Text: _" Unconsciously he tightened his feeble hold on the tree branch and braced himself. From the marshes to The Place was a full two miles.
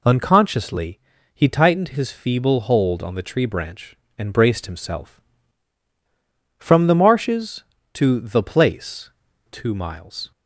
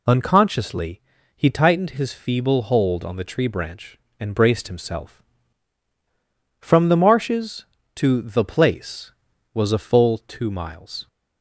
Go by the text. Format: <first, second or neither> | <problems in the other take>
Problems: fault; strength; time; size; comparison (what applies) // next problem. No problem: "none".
second | pauses between "Unconsciously" and "he"; slight; at 0.9 s; 0.34 s long; slight in the second // skips "was a full"; at 9.2 s